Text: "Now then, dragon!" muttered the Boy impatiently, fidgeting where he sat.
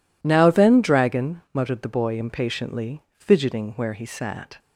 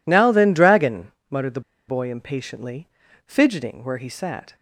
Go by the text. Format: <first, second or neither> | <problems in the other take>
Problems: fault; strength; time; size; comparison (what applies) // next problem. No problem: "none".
first | pauses between "the" and "Boy"; slight; at 1.6 s; 0.28 s long